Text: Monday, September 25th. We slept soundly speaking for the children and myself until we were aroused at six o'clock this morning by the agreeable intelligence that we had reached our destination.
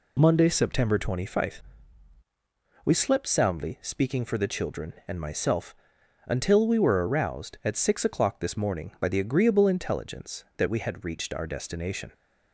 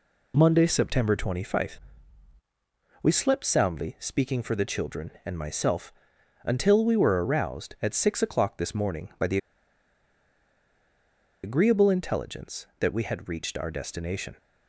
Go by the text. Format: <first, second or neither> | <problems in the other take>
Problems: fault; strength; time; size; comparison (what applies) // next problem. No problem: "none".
first | pauses between "myself" and "until"; noticeable; at 5.9 s; 0.50 s long; noticeable in the first // pauses between "the" and "agreeable"; strong; at 9.3 s; 2.0 s long